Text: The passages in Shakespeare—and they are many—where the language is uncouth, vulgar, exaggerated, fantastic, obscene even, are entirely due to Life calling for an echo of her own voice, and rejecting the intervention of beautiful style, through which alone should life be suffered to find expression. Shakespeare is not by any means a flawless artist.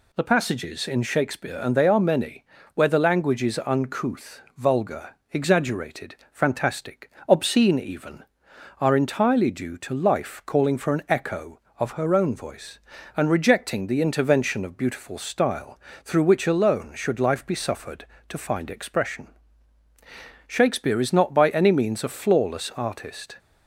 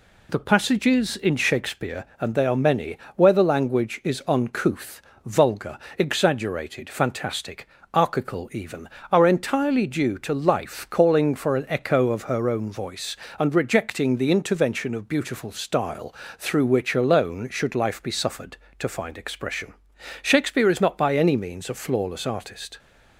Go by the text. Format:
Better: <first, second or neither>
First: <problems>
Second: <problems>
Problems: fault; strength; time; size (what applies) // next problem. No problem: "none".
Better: first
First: none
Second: says "archical" for "obscene"; at 7.9 s